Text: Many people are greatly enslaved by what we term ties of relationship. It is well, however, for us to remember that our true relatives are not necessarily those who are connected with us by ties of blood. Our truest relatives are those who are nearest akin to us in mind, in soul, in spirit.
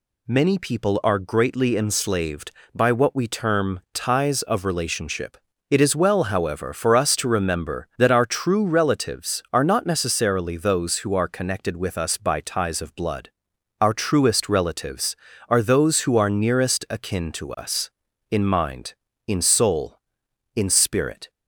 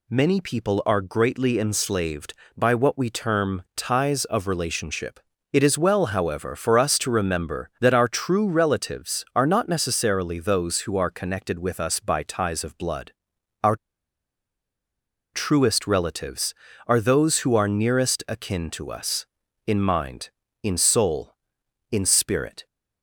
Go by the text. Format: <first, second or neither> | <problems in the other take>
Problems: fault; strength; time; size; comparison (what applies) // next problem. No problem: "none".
first | pauses between "Our" and "truest"; strong; at 13.7 s; 1.5 s long